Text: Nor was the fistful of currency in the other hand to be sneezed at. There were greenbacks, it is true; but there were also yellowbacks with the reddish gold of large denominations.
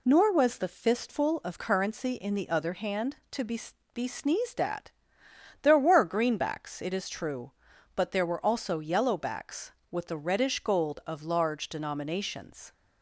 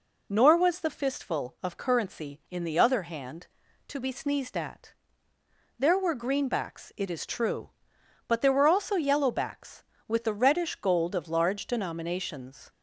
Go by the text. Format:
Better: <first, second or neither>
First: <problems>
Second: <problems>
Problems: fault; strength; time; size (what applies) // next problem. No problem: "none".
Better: second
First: says "be" twice; at 3.9 s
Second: none